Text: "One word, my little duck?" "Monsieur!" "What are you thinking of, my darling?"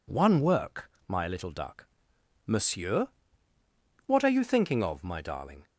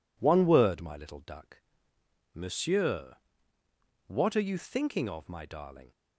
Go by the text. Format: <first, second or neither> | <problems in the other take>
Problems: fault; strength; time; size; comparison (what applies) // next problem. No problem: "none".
second | says "work" for "word"; at 0.4 s